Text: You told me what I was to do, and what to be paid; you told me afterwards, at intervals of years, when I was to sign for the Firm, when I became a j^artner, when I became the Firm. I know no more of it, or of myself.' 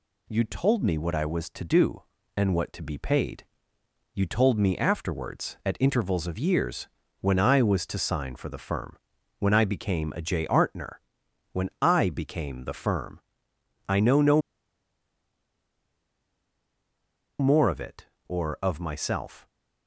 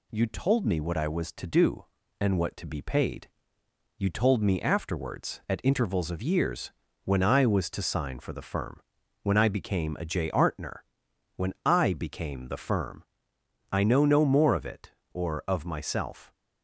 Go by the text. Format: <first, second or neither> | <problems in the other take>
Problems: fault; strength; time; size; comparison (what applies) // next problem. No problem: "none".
second | pauses between "no" and "more"; strong; at 14.4 s; 2.9 s long